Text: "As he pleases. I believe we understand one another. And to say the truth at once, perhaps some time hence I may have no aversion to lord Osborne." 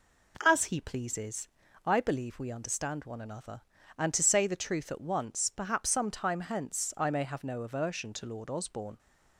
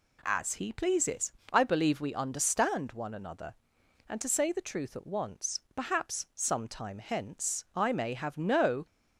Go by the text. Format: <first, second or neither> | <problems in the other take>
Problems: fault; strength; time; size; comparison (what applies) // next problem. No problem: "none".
first | stops before "aversion to lord Osborne"; at 8.8 s